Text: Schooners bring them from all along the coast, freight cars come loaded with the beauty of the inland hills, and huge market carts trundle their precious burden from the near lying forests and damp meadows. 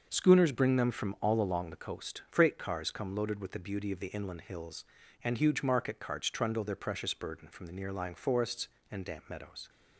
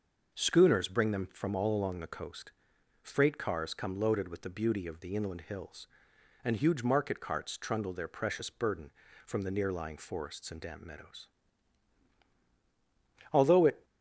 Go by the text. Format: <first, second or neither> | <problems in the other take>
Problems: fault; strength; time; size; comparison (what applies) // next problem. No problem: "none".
first | starts louder than the rest; noticeable; until 1.3 s; 6 dB; noticeable in the first // goes on to say "Although it"; from 13.3 s on; 0.52 s long